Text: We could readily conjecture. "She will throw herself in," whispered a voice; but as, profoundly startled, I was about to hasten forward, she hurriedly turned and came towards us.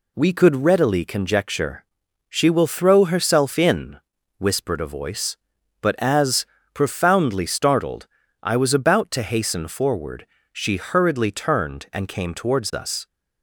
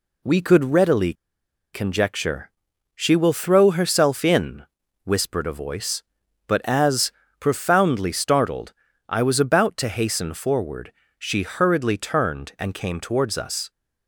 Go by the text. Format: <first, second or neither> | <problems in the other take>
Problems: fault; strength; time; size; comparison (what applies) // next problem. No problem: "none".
first | pauses between "readily" and "conjecture"; noticeable; at 1.1 s; 0.60 s long